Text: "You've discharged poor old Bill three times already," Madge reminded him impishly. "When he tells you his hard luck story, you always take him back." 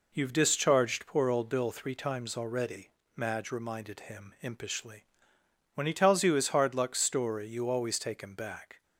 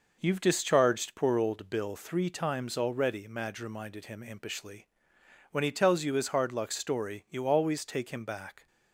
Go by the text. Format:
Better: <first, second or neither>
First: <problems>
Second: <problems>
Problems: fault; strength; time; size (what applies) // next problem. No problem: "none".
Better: neither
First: none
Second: none